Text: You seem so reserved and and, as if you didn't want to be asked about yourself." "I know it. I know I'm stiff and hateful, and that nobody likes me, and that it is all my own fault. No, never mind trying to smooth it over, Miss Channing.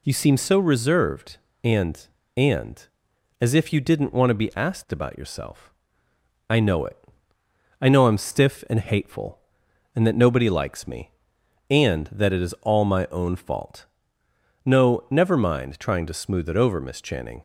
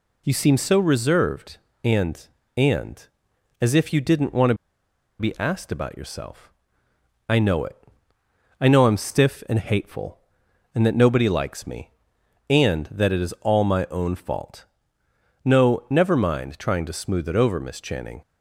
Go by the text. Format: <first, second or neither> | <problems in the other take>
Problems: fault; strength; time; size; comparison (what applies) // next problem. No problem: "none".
first | pauses between "to" and "be"; noticeable; at 4.5 s; 0.64 s long